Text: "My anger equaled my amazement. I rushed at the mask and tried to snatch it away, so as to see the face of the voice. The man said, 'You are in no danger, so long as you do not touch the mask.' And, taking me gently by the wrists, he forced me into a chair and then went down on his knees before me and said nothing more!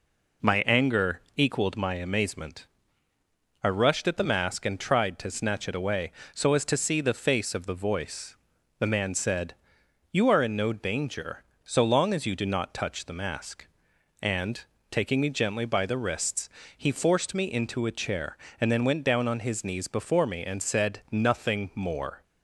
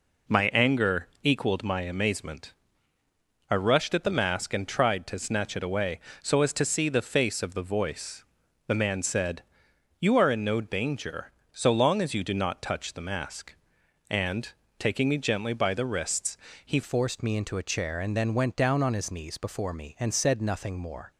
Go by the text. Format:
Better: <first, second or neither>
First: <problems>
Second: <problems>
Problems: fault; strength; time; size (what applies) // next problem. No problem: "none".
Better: first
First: pauses between "anger" and "equaled"; slight; at 1.1 s; 0.16 s long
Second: pauses between "anger" and "equaled"; slight; at 1.0 s; 0.16 s long // changes voice at "forced"; from 16.8 s on; 4.3 s long